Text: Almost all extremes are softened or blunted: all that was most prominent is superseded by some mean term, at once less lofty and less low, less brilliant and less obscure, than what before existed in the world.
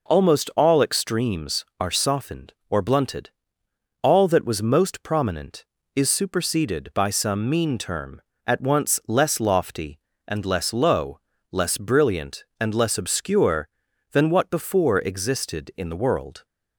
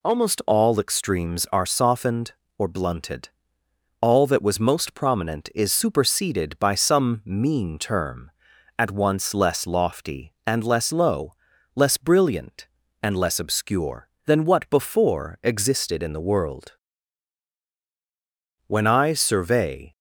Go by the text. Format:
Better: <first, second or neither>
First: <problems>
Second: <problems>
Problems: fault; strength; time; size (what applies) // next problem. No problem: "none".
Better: first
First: none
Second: goes on to say "When I survey"; noticeable; from 18.6 s on; 1.3 s long